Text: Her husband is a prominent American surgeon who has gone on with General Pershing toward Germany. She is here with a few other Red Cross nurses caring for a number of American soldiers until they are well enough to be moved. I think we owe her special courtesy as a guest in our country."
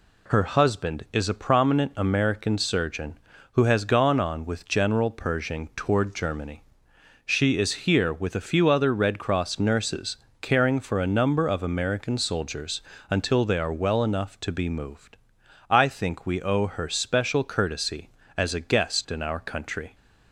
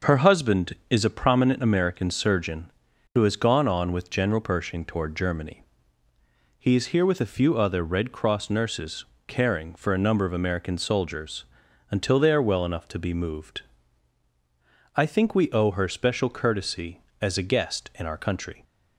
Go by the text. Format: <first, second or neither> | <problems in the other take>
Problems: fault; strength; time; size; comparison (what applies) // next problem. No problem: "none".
first | says "He" for "She"; at 6.5 s // pauses between "nurses" and "caring"; slight; at 9.0 s; 0.22 s long; slight in the first // pauses between "soldiers" and "until"; noticeable; at 11.4 s; 0.46 s long; slight in the first